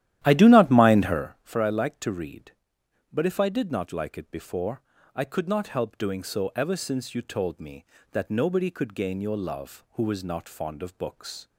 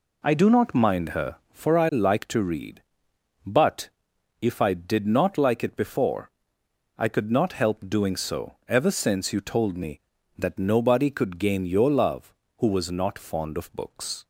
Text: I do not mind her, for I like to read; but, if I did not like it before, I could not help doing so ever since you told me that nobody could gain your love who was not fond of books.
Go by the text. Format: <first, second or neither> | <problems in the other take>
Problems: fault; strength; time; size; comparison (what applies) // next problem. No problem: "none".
second | starts louder than the rest; strong; until 1.3 s; 12.5 dB